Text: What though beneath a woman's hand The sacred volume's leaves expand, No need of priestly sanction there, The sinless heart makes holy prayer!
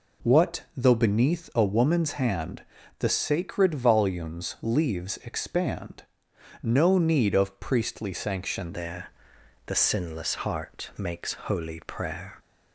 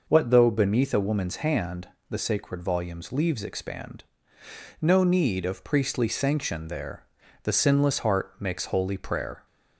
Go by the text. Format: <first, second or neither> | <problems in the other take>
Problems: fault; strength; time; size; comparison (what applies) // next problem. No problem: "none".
second | pauses between "hand" and "The"; slight; at 2.6 s; 0.36 s long; slight in the second // changes voice at "there"; from 8.7 s on; 3.6 s long